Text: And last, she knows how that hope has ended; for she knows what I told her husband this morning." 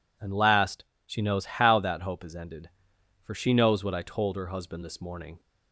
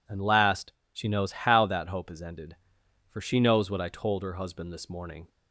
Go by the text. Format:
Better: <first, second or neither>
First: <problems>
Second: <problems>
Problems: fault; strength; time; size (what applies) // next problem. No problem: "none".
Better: neither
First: none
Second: none